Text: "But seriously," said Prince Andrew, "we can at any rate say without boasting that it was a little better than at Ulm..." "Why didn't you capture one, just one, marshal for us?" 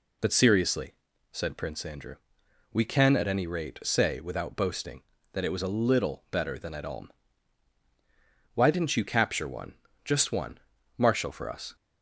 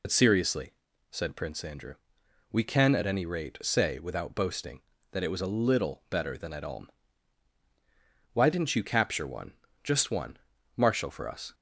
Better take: first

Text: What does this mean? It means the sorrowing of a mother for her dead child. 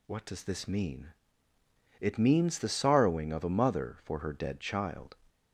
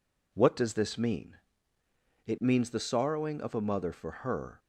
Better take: first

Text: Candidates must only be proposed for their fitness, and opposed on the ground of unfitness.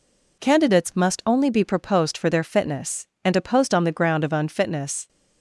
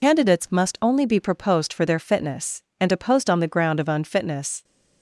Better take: first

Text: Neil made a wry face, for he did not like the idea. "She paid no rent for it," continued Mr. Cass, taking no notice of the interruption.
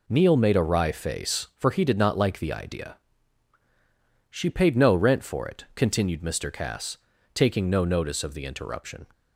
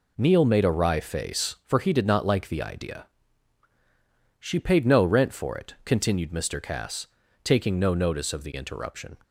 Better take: neither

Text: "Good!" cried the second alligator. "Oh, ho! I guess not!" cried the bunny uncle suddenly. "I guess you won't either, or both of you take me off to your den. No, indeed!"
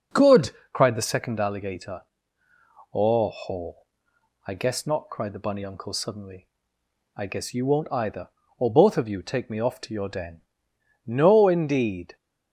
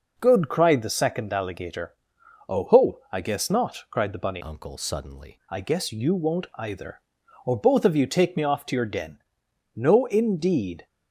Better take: first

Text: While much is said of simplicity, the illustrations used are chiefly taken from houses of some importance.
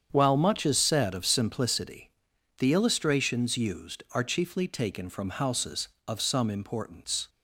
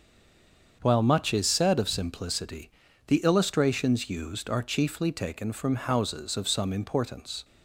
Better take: first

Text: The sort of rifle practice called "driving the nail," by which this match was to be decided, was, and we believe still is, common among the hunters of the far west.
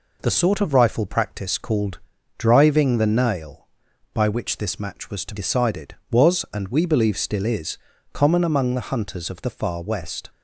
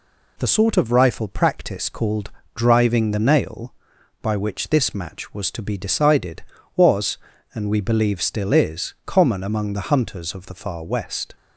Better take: second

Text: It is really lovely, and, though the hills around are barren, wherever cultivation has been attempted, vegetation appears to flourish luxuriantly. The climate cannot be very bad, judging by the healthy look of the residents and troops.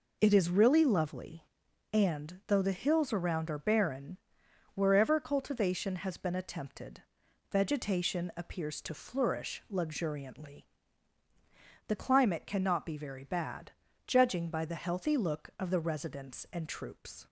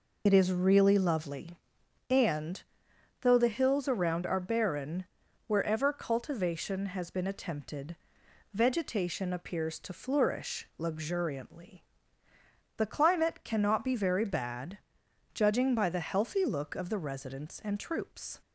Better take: first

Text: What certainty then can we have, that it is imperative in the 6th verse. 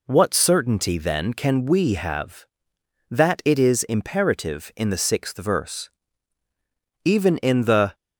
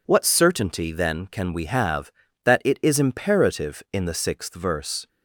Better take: second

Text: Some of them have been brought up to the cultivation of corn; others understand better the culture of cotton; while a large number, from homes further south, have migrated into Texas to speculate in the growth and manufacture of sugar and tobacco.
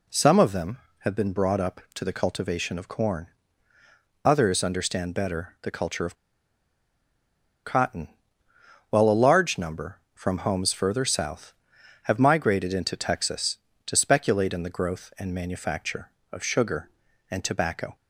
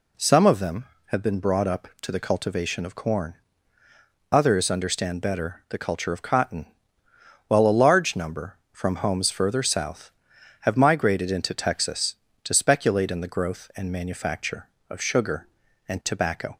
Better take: second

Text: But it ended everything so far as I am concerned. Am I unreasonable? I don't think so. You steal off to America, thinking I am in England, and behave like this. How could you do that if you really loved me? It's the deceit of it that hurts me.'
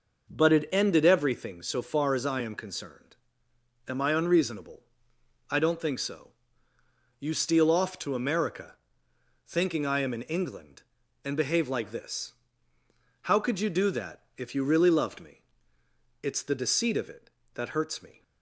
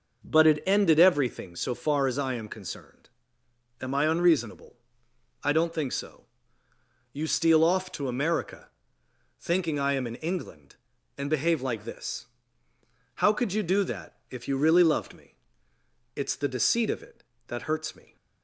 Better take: neither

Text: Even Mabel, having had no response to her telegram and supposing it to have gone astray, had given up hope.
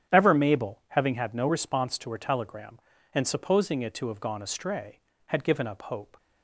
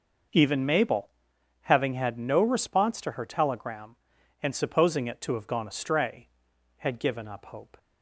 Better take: second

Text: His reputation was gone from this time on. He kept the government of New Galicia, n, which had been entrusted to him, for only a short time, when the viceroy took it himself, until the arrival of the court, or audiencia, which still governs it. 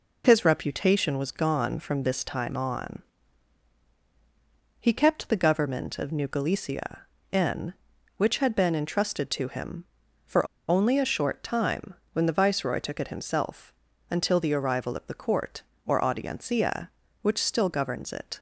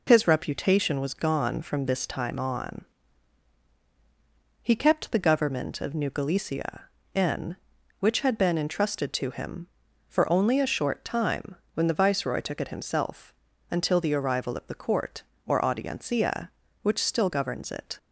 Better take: second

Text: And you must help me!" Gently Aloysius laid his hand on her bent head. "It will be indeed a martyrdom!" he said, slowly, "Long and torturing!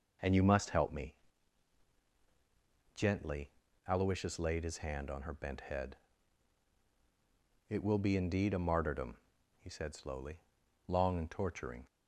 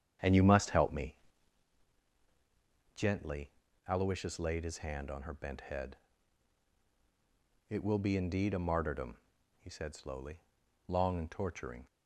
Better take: first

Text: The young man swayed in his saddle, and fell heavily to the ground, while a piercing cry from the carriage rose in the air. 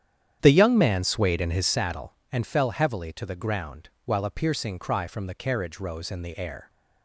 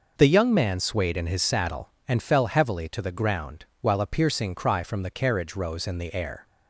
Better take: second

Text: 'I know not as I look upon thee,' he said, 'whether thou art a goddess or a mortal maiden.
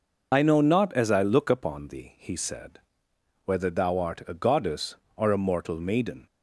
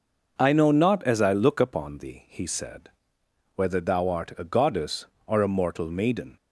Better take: second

